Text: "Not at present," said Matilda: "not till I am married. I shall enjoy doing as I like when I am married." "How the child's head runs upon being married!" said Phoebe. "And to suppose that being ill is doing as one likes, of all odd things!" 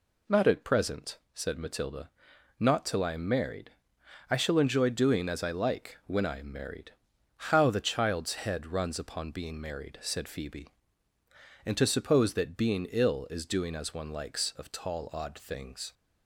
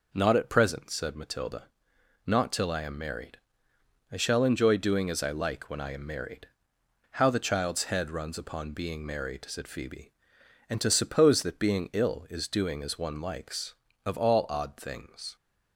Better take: second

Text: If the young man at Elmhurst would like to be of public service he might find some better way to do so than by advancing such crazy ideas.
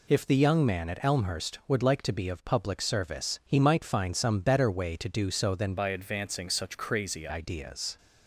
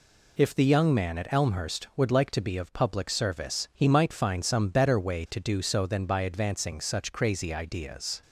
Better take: second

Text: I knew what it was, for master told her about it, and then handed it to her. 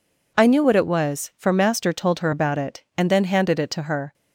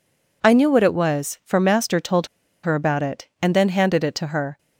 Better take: first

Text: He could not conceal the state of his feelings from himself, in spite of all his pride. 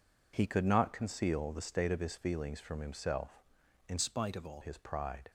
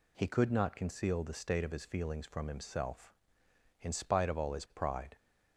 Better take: second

